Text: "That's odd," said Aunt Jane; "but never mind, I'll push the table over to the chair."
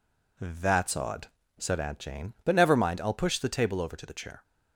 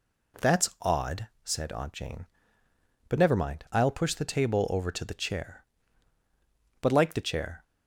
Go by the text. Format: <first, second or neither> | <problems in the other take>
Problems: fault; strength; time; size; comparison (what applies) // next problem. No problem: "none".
first | goes on to say "But like the chair"; noticeable; from 6.8 s on; 0.82 s long